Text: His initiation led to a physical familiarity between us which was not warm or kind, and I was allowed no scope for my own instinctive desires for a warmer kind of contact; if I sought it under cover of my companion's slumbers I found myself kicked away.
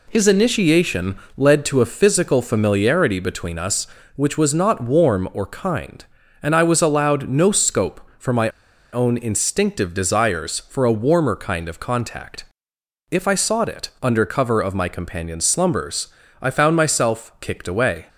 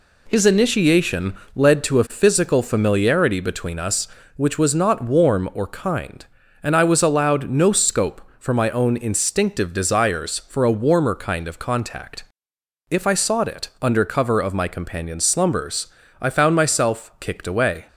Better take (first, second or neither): second